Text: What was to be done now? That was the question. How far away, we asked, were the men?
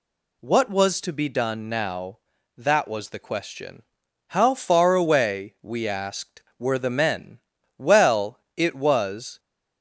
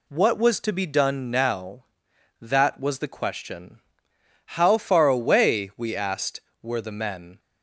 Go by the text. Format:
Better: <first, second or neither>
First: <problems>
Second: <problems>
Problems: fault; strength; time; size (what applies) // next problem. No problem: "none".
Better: second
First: goes on to say "Well it was"; from 7.7 s on; 1.6 s long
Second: none